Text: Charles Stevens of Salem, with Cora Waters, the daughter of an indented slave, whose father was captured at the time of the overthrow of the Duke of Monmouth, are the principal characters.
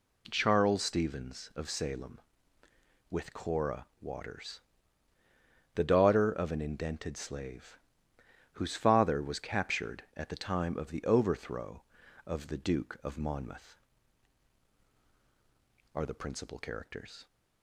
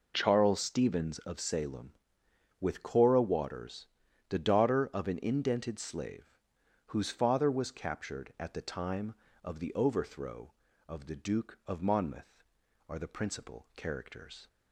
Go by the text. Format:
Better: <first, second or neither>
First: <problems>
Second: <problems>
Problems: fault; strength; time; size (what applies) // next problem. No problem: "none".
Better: neither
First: none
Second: none